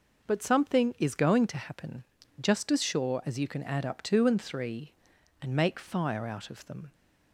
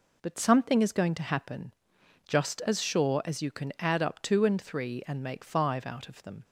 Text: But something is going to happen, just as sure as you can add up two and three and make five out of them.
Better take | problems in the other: second | says "fire" for "five"; at 5.7 s

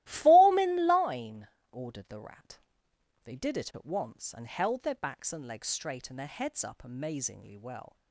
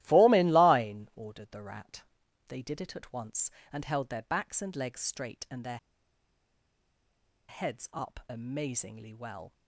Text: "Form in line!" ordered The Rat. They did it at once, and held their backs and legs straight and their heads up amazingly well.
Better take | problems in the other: first | starts louder than the rest; strong; until 1.0 s; 15 dB; strong in the first // pauses between "their" and "heads"; strong; at 5.7 s; 1.7 s long

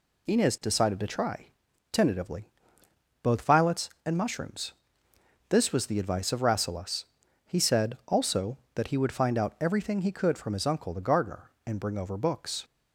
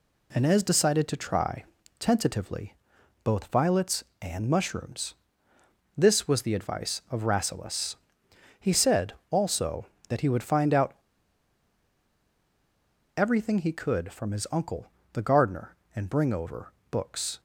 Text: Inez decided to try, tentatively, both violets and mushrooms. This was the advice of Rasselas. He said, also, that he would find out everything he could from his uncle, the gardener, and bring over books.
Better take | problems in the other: first | pauses between "out" and "everything"; strong; at 10.9 s; 2.2 s long // pauses between "over" and "books"; slight; at 16.7 s; 0.18 s long

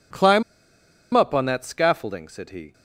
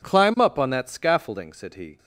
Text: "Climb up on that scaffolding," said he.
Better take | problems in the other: second | pauses between "Climb" and "up"; noticeable; at 0.4 s; 0.71 s long

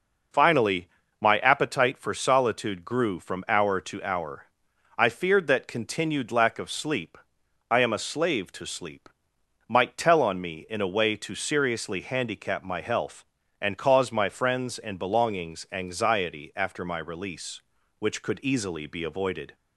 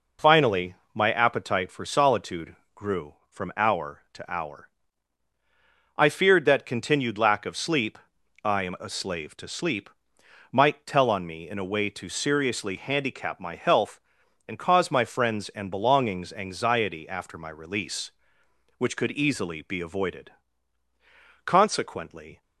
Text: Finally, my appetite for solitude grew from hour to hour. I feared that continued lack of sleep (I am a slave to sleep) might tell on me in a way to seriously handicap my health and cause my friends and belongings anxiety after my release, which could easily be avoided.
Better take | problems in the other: first | pauses between "solitude" and "grew"; slight; at 2.5 s; 0.20 s long // goes on to say "Consequently"; noticeable; from 21.4 s on; 0.96 s long

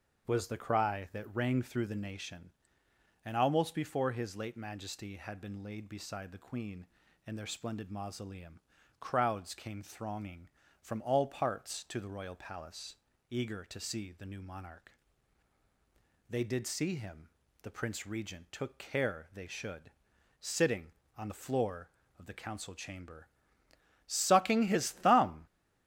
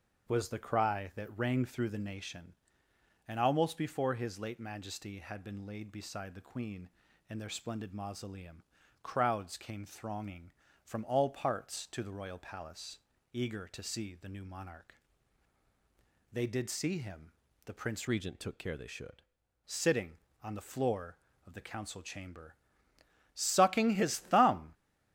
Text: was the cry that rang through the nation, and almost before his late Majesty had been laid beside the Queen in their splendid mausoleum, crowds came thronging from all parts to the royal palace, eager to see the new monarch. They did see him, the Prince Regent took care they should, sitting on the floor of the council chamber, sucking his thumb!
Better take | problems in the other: first | starts louder than the rest; until 1.3 s; 6.5 dB; also in the first // changes voice from "Regent" to "should"; from 18.0 to 19.2 s; 1.2 s long

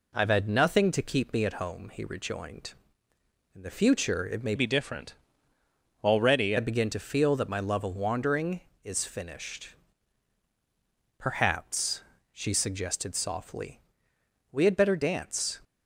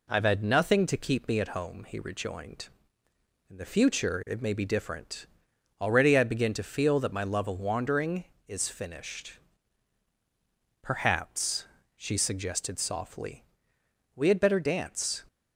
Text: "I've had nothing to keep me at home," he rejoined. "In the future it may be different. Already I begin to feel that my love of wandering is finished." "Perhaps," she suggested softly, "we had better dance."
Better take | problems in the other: second | changes voice from "be" to "Already"; from 4.5 to 6.5 s; 2.0 s long

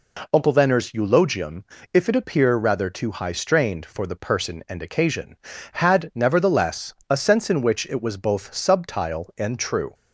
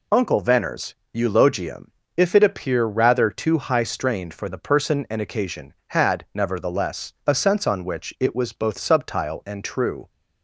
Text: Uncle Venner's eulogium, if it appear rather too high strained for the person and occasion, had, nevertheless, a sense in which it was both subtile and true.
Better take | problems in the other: first | pauses between "Venner's" and "eulogium"; slight; at 0.9 s; 0.20 s long // says "on" for "in"; at 7.6 s

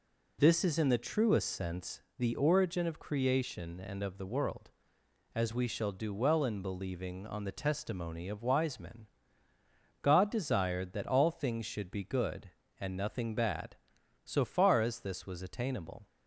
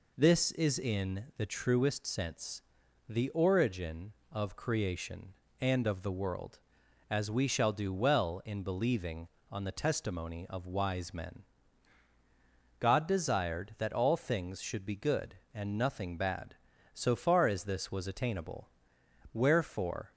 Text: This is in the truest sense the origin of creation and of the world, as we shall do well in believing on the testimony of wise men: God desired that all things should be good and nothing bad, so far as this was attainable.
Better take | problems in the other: first | pauses between "sense" and "the"; noticeable; at 2.6 s; 0.46 s long; slight in the first // goes on to say "Wherefore"; noticeable; from 19.3 s on; 0.80 s long

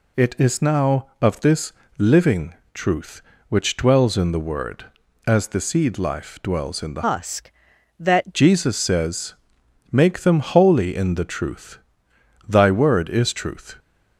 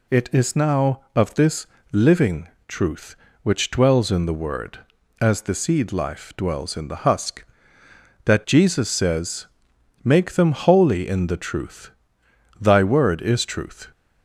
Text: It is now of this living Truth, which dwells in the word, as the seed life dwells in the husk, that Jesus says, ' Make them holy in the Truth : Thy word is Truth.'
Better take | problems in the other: second | pauses between "this" and "living"; slight; at 1.7 s; 0.24 s long; slight in the second // pauses between "living" and "Truth"; slight; at 2.5 s; 0.20 s long; slight in the second // changes voice from "husk" to "that"; from 7.0 to 8.3 s; 1.3 s long

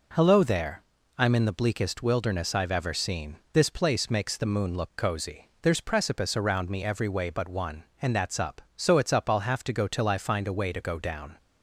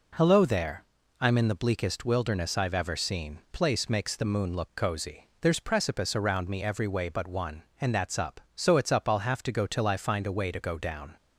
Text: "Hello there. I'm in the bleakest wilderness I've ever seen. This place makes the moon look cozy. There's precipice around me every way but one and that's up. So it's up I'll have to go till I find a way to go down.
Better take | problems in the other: first | skips "This"; at 3.4 s

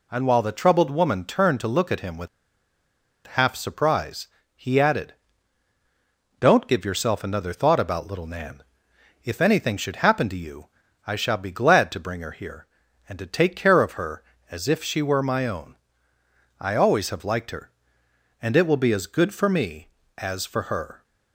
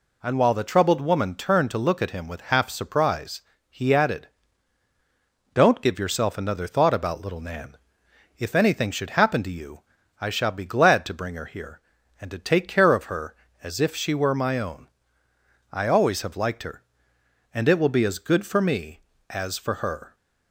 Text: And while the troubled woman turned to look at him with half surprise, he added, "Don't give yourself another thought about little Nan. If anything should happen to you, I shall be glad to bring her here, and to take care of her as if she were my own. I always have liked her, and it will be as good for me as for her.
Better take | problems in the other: second | pauses between "with" and "half"; at 2.2 s; 0.98 s long

